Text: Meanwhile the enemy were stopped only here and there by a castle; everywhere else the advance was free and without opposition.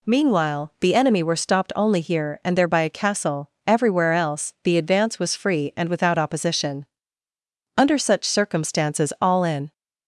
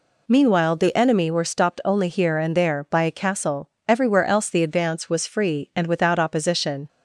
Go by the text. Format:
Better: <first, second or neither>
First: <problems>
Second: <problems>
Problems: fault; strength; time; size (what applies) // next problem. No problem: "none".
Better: second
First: goes on to say "Under such circumstances all in"; strong; from 7.7 s on; 1.9 s long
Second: none